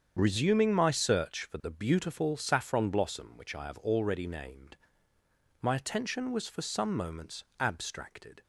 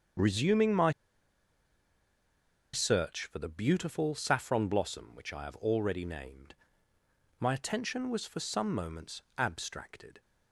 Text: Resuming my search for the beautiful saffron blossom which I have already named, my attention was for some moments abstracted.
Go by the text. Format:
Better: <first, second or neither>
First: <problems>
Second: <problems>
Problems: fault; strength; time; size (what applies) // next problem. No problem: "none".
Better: first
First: starts louder than the rest; strong; until 1.1 s; 7.5 dB // pauses between "moments" and "abstracted"; slight; at 7.4 s; 0.16 s long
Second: starts louder than the rest; strong; until 3.0 s; 7.5 dB // pauses between "my" and "search"; strong; at 0.9 s; 1.8 s long // pauses between "moments" and "abstracted"; slight; at 9.2 s; 0.16 s long